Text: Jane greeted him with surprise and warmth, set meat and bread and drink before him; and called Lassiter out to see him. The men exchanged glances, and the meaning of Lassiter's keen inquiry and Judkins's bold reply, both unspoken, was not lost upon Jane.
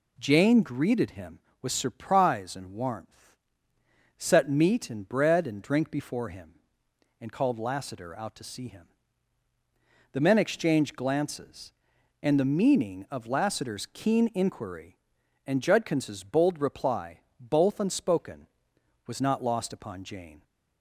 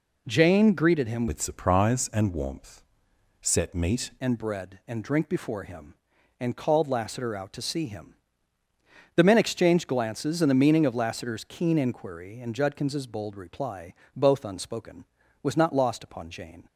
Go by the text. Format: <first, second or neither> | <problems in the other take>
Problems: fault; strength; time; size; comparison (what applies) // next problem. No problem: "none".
first | changes voice from "with" to "meat"; from 1.2 to 4.0 s; 2.8 s long